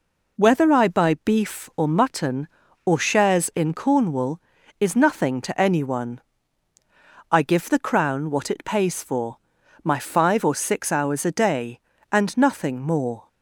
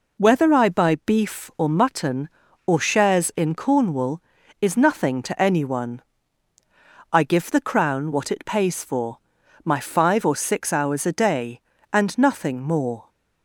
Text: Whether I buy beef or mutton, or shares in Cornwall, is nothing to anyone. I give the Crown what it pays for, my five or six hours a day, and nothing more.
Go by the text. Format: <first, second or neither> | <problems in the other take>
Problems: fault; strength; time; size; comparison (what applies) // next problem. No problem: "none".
neither | none